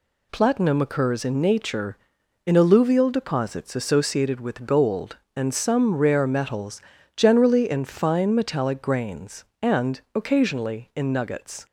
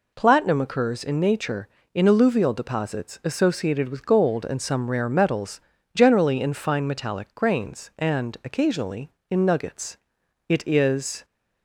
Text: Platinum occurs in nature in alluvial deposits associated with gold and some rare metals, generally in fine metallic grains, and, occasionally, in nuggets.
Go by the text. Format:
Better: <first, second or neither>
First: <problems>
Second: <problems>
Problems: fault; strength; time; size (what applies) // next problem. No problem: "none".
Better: first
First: none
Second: goes on to say "It is"; noticeable; from 10.4 s on; 0.76 s long